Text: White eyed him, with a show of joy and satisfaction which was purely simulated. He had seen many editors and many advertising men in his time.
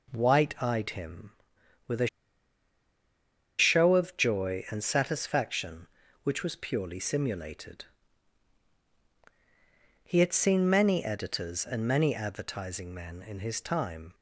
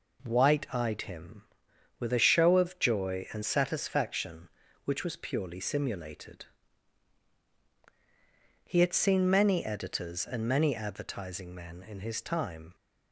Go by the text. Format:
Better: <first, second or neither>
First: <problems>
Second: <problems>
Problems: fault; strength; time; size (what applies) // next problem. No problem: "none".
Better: second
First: pauses between "a" and "show"; strong; at 2.0 s; 1.5 s long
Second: none